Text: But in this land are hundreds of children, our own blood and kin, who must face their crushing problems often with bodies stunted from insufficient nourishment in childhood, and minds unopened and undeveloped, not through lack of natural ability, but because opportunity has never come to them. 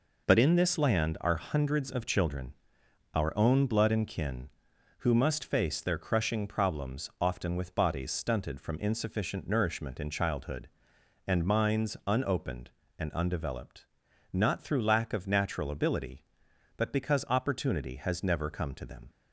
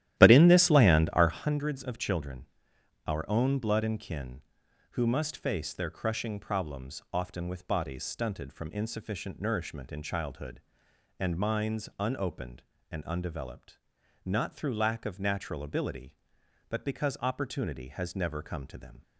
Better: first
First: none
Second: starts louder than the rest; strong; until 1.6 s; 13 dB

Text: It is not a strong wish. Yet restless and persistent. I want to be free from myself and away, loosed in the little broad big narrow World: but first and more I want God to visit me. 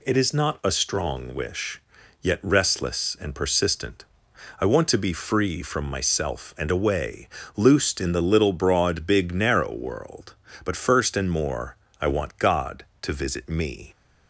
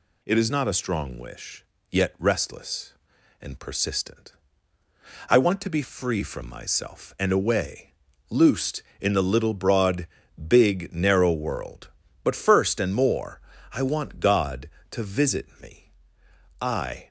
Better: first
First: pauses between "more" and "I"; slight; at 11.7 s; 0.24 s long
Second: pauses between "broad" and "big"; at 10.0 s; 0.40 s long // pauses between "more" and "I"; slight; at 13.4 s; 0.32 s long // goes on to say "I"; slight; from 16.6 s on; 0.46 s long

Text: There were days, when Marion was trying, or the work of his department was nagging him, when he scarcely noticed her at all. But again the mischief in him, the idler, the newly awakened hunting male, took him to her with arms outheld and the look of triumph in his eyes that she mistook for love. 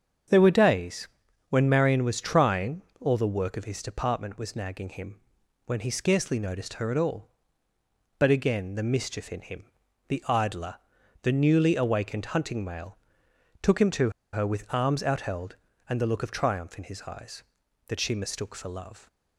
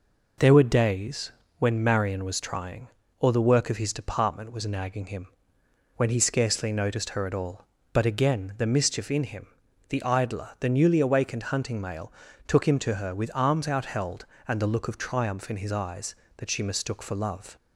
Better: second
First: starts louder than the rest; strong; until 1.7 s; 7.5 dB // pauses between "to" and "her"; slight; at 14.1 s; 0.22 s long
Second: none

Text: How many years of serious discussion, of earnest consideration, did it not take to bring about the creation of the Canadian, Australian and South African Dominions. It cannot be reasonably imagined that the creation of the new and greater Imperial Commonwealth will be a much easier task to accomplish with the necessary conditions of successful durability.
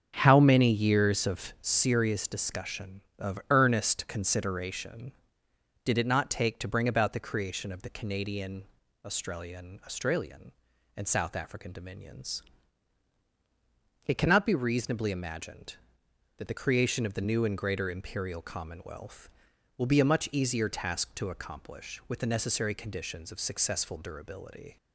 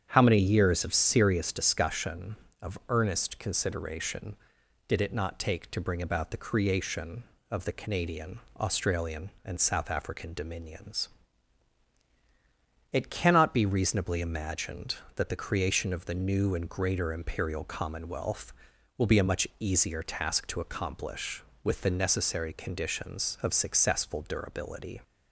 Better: second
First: starts louder than the rest; strong; until 1.1 s; 7.5 dB // says "Australian" twice; at 9.8 s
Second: starts louder than the rest; strong; until 1.1 s; 8.5 dB

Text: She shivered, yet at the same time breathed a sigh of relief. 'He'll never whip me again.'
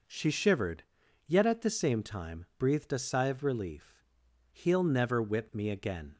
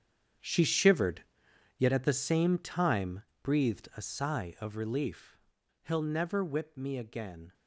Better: first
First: none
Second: gets quieter; strong; throughout; 14 dB // pauses between "time" and "breathed"; slight; at 3.2 s; 0.18 s long

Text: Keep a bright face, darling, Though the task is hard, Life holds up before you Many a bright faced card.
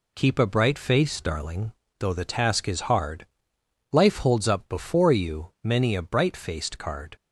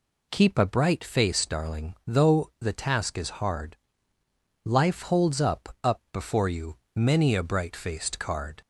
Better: first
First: none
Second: says "up" twice; at 5.8 s // pauses between "you" and "Many"; slight; at 6.7 s; 0.18 s long

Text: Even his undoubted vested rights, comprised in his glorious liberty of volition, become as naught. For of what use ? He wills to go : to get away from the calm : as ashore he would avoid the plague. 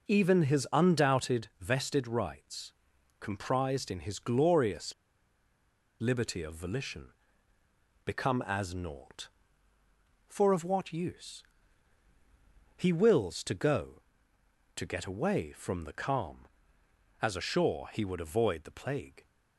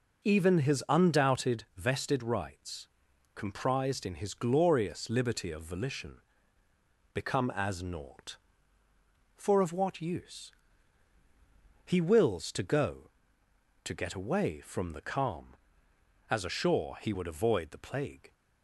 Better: second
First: pauses between "glorious" and "liberty"; at 4.9 s; 1.0 s long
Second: none

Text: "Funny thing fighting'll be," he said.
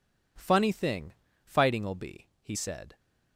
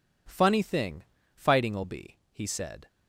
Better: neither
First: pauses between "thing" and "fighting'll"; slight; at 1.1 s; 0.30 s long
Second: pauses between "thing" and "fighting'll"; slight; at 1.0 s; 0.30 s long

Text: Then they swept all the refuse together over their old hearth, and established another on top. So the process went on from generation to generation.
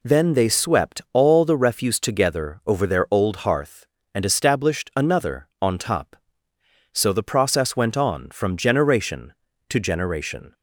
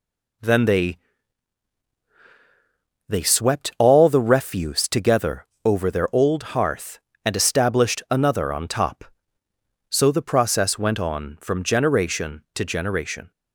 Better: first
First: none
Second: says "they" twice; at 3.1 s // pauses between "together" and "over"; slight; at 5.4 s; 0.18 s long

